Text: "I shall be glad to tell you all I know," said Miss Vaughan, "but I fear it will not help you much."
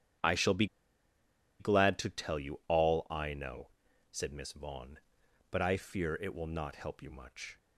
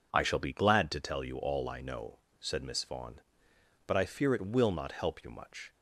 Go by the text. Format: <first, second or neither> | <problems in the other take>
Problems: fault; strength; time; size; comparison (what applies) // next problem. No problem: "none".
second | starts louder than the rest; strong; until 2.1 s; 9.5 dB // pauses between "be" and "glad"; noticeable; at 0.6 s; 0.94 s long